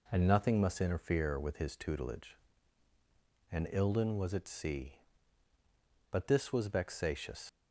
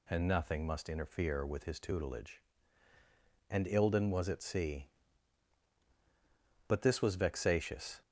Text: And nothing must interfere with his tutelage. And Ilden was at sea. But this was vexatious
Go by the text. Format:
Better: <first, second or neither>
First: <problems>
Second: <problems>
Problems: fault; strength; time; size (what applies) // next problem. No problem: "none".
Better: second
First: leaves "vexatious" unfinished; at 7.4 s; 80 ms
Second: none